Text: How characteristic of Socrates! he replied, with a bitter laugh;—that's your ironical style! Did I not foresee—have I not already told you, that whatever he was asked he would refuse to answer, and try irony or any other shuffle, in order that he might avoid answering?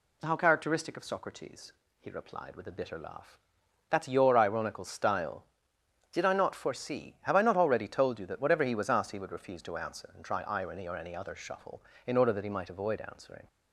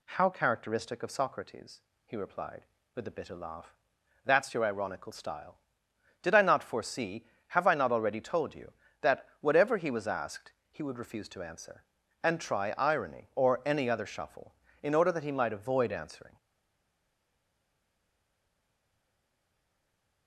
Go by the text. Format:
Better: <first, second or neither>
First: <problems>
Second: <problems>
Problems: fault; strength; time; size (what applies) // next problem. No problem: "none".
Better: first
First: none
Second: pauses between "asked" and "he"; slight; at 10.5 s; 0.18 s long // stays silent after the last word; strong; from 16.3 s on; 3.9 s long